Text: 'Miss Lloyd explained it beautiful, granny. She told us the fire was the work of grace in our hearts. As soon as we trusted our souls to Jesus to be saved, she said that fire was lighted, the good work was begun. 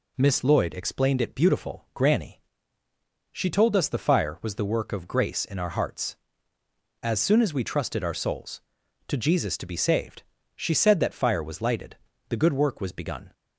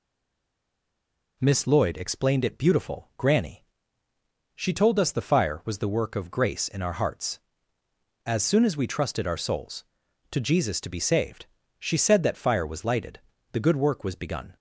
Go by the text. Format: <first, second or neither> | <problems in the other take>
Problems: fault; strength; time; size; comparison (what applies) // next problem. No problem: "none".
first | stays silent before the first word; noticeable; until 1.3 s; 1.3 s long